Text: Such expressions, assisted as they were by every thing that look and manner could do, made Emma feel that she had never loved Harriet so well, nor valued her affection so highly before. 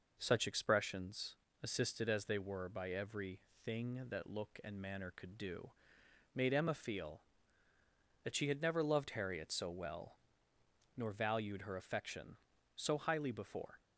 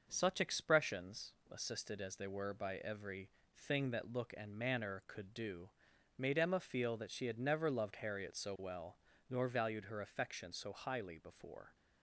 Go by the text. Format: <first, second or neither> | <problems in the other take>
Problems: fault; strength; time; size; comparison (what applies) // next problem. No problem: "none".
neither | pauses between "every" and "thing"; slight; the same in both